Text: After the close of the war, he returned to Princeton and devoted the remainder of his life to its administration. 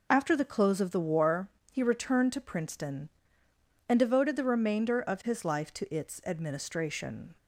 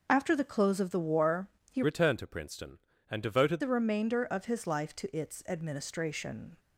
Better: first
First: none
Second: changes voice from "returned" to "devoted"; from 1.8 to 3.6 s; 1.8 s long

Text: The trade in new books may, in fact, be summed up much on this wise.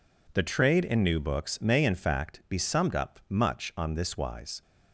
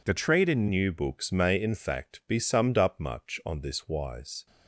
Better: first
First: none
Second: changes voice at "new"; from 0.6 s on; 3.8 s long

